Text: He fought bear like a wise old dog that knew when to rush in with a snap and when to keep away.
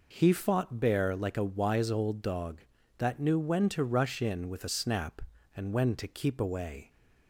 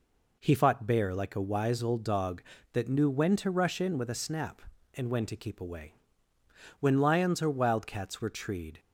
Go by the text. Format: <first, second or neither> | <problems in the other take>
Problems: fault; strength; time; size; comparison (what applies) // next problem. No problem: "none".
first | goes on to say "When lions or wildcats were treed"; strong; from 6.7 s on; 2.0 s long